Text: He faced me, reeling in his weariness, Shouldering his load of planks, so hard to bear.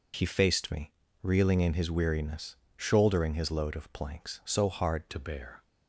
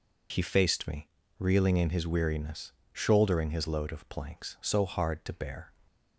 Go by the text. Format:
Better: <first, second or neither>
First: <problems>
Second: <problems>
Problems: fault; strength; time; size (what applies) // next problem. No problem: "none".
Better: second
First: changes voice at "to"; from 5.0 s on; 0.6 s long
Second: none